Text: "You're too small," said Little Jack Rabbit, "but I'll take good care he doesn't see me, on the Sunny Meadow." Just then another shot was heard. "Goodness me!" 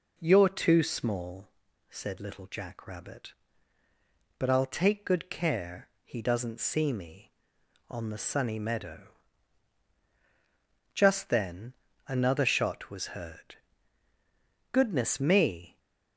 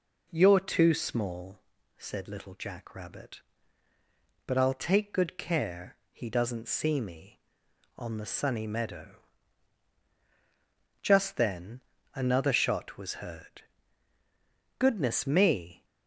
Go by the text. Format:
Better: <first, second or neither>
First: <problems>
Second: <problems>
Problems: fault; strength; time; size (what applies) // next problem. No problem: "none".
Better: neither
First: pauses between "care" and "he"; slight; at 5.8 s; 0.16 s long // pauses between "then" and "another"; slight; at 11.7 s; 0.34 s long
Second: pauses between "care" and "he"; slight; at 5.9 s; 0.16 s long // pauses between "then" and "another"; slight; at 11.7 s; 0.34 s long